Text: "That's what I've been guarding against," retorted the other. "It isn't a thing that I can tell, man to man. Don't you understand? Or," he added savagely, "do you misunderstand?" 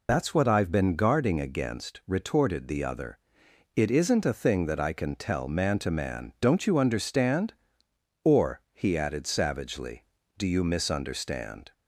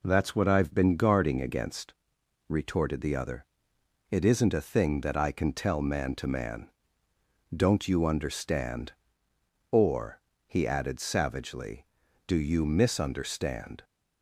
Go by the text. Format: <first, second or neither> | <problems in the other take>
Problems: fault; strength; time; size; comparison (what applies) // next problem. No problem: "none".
second | loses the start of "That's"; at 0.0 s; 100 ms